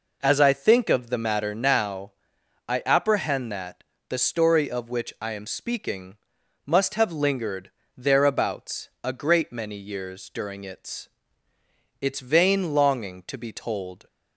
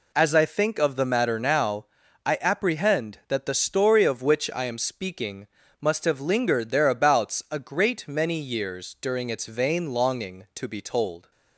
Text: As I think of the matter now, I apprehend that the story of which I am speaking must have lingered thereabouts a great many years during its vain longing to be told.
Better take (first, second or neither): second